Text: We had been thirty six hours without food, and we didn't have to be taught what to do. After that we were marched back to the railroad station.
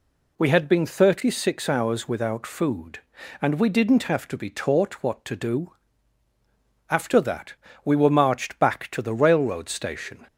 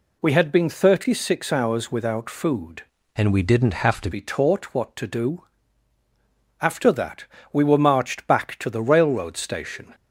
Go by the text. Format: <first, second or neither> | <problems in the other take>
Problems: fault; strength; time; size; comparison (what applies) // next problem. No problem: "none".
first | changes voice from "and" to "to"; from 3.1 to 4.0 s; 0.9 s long // pauses between "that" and "we"; slight; at 7.2 s; 0.28 s long; slight in the first